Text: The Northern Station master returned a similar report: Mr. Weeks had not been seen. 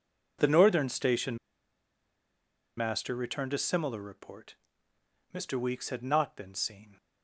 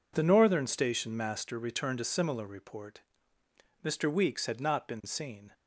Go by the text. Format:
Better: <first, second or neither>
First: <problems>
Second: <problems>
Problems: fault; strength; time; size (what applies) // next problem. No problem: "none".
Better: second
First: pauses between "Station" and "master"; strong; at 1.3 s; 1.4 s long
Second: none